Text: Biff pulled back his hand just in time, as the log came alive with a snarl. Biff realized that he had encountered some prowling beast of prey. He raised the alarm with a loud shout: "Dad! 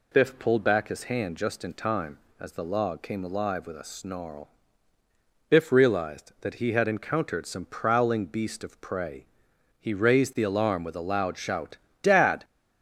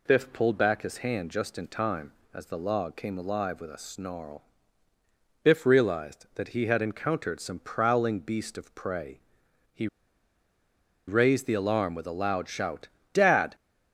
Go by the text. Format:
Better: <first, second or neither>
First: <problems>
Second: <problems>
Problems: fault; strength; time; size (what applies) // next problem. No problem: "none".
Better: first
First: none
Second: pauses between "He" and "raised"; at 9.8 s; 1.2 s long